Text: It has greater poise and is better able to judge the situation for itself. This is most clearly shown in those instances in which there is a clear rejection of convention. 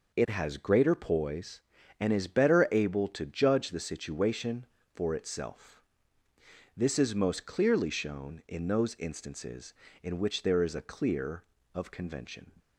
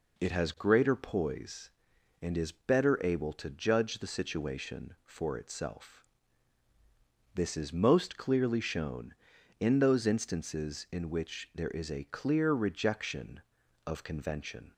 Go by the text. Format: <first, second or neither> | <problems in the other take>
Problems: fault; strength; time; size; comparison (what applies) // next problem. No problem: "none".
second | skips "rejection"; at 11.5 s